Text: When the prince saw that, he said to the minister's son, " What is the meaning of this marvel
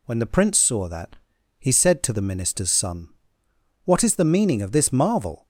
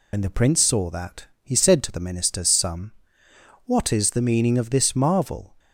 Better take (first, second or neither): first